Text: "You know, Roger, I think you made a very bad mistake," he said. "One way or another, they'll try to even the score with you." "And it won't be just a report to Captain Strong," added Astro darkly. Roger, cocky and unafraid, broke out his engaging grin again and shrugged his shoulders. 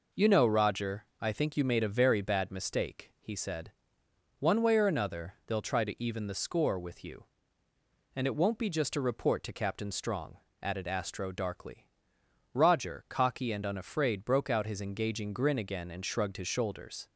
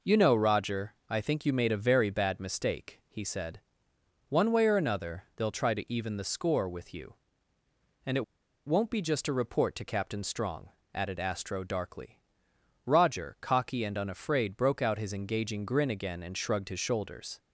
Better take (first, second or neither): first